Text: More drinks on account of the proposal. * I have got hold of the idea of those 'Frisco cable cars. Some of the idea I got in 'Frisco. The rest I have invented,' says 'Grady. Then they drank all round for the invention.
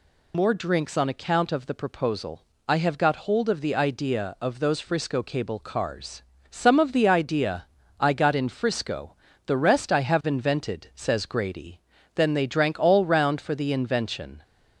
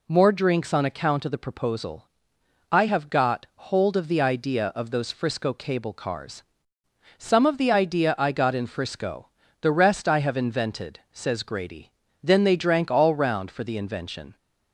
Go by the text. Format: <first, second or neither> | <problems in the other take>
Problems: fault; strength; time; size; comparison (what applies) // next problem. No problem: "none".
second | loses the start of "More"; at 0.3 s; 35 ms // pauses between "idea" and "I"; slight; at 7.6 s; 0.32 s long